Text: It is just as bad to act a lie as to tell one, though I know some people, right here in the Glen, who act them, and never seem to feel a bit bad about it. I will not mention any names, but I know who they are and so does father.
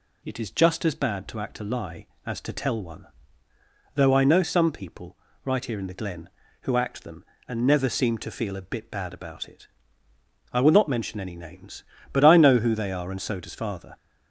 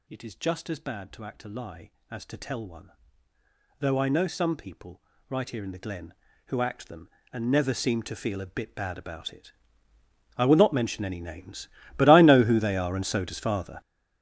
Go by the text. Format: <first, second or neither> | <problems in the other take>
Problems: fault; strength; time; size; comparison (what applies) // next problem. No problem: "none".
first | gets louder; strong; throughout; 13 dB